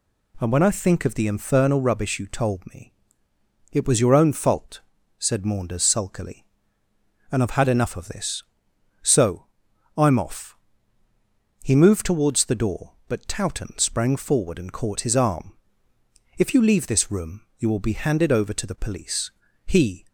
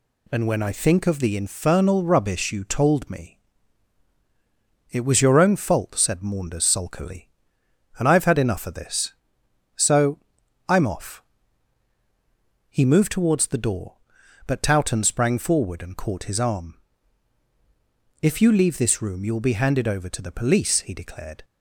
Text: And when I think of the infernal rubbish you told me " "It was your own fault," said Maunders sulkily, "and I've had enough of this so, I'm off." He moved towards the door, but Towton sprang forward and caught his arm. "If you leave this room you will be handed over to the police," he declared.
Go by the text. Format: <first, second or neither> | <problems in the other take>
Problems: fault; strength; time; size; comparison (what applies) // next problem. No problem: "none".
second | pauses between "room" and "you"; slight; at 17.4 s; 0.16 s long // stops before "declared"; at 20.0 s